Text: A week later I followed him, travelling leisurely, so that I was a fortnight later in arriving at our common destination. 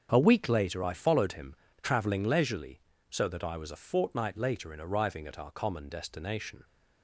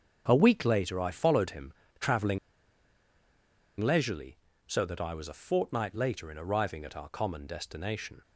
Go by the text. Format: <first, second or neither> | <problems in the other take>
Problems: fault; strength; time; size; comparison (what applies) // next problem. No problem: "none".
first | starts louder than the rest; strong; until 1.2 s; 7.5 dB; strong in the first // pauses between "travelling" and "leisurely"; strong; at 2.3 s; 1.4 s long